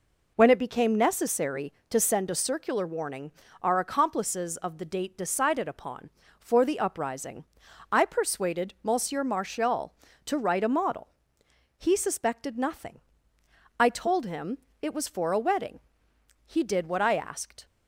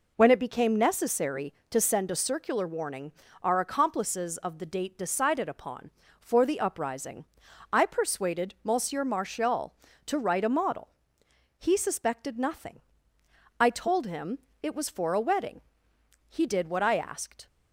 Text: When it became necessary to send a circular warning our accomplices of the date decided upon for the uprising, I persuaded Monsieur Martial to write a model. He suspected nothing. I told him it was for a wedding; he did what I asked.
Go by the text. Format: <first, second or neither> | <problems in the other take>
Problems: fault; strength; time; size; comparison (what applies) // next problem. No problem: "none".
neither | pauses between "warning" and "our"; slight; the same in both // pauses between "him" and "it"; slight; the same in both